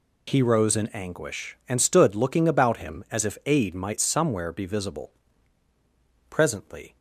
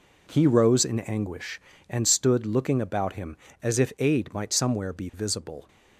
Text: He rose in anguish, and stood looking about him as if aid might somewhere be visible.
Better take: second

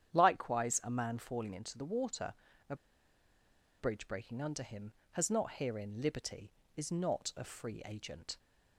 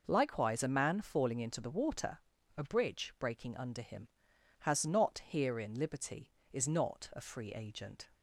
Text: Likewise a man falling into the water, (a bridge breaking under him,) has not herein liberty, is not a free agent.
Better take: second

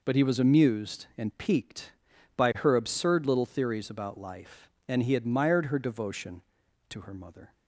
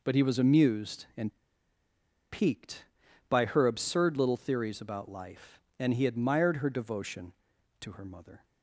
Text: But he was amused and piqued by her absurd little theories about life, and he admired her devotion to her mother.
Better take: first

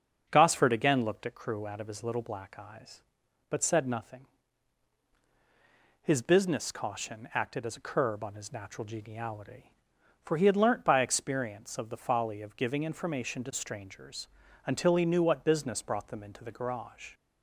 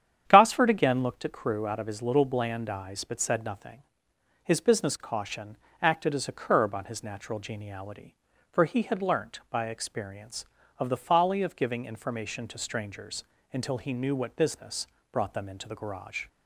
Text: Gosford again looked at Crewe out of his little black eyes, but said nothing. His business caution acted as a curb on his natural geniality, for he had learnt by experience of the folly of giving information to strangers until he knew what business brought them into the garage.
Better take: first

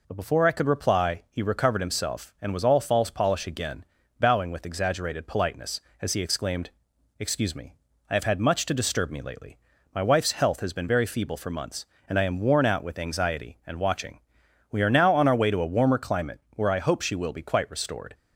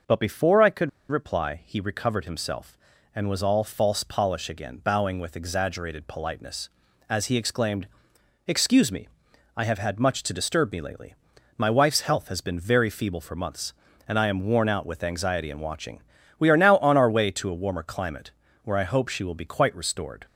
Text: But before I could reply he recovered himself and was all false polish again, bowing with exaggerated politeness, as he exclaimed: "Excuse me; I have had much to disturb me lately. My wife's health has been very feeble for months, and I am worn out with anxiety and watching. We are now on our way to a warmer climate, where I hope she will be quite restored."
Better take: first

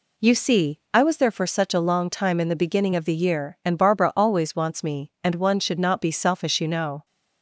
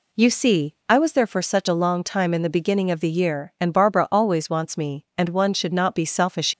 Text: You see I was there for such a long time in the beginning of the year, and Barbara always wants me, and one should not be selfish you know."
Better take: first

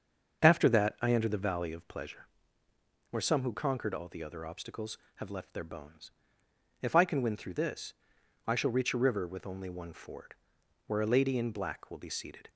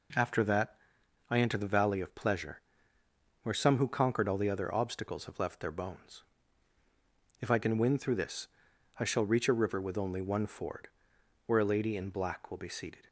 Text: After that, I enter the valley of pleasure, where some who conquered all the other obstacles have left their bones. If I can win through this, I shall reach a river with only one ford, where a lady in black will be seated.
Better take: second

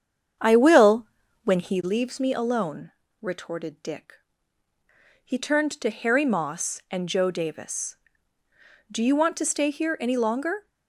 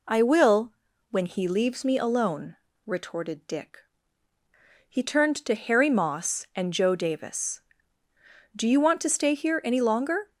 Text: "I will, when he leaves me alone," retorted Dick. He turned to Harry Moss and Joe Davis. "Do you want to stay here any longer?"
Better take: second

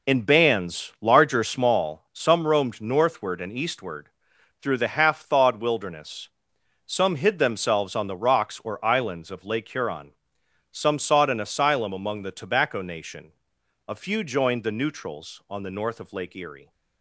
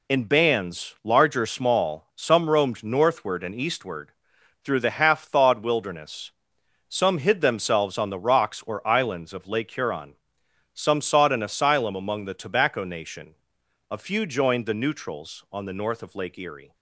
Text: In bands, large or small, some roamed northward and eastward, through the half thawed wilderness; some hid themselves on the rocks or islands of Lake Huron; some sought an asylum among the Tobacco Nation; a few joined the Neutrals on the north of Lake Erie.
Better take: second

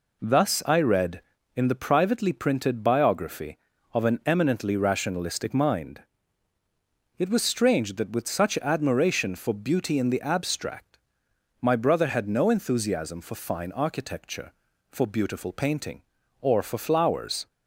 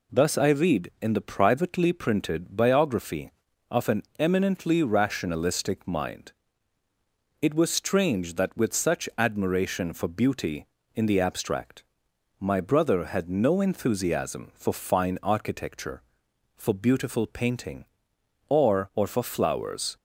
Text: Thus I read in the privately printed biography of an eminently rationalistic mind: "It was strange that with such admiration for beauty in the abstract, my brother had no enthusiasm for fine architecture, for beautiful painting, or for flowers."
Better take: first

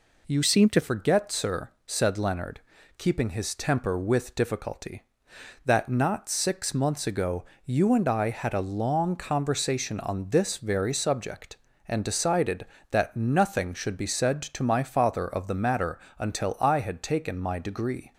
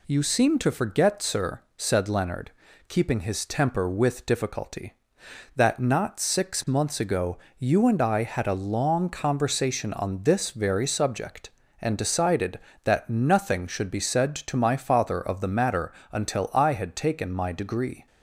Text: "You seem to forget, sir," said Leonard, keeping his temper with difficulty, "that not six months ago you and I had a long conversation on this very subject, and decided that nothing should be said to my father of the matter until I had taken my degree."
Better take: second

